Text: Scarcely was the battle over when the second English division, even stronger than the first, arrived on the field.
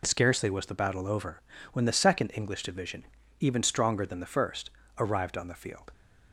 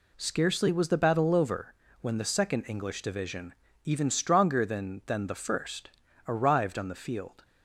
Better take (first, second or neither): first